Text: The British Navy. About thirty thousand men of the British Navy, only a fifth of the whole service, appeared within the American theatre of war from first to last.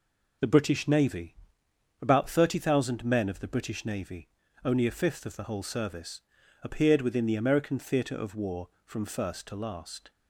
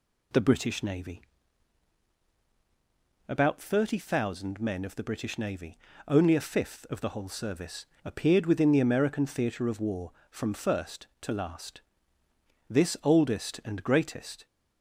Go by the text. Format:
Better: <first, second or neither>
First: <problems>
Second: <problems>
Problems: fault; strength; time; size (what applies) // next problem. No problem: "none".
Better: first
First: none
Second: goes on to say "This oldest and greatest"; strong; from 12.6 s on; 1.7 s long